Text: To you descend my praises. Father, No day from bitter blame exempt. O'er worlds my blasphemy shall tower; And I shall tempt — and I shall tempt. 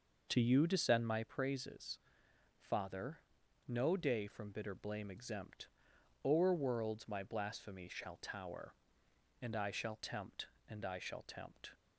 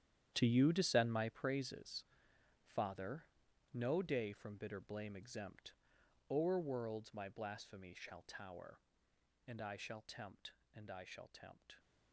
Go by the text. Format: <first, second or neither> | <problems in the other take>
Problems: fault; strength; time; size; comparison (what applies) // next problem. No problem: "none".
first | gets quieter; strong; throughout; 15 dB